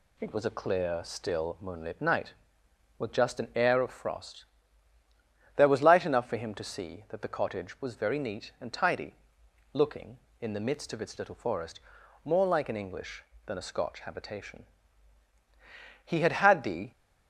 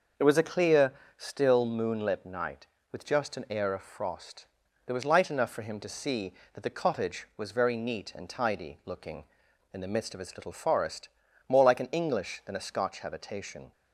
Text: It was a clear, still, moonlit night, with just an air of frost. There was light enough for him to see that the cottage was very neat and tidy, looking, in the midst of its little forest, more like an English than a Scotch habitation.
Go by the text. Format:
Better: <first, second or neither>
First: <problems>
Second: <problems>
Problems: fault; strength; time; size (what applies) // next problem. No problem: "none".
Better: second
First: goes on to say "He had had the"; noticeable; from 16.0 s on; 0.86 s long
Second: none